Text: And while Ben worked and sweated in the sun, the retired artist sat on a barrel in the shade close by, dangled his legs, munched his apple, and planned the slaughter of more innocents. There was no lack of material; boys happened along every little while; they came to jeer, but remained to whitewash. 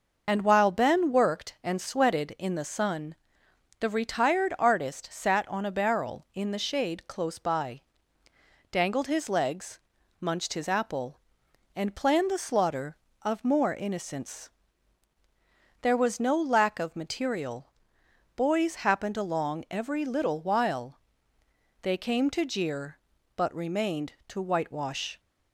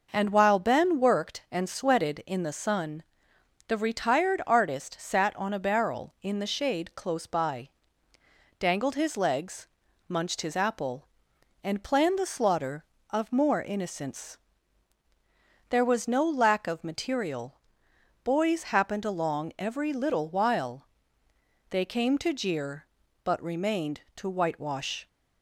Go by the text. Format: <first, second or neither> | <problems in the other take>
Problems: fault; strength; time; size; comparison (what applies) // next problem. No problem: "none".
second | loses the start of "And"; at 0.2 s; 65 ms